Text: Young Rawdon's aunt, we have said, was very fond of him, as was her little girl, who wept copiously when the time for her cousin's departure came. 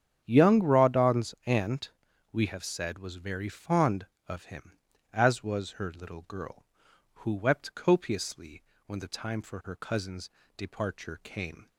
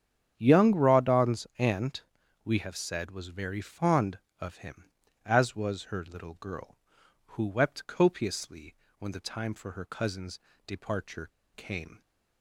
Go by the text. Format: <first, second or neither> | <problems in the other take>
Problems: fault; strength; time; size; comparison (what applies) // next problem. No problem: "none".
first | starts louder than the rest; strong; until 1.3 s; 8.5 dB; strong in the first // pauses between "copiously" and "when"; slight; at 8.7 s; 0.24 s long; slight in the first // pauses between "cousin's" and "departure"; slight; at 10.4 s; 0.26 s long; slight in the first // pauses between "departure" and "came"; slight; at 11.2 s; 0.25 s long